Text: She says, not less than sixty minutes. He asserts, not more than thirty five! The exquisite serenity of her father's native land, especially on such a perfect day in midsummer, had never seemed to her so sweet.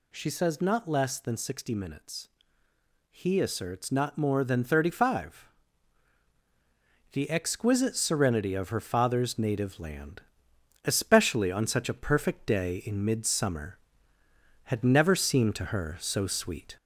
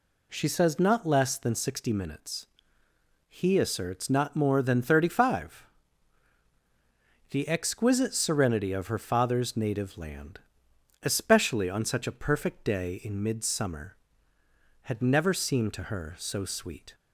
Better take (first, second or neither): second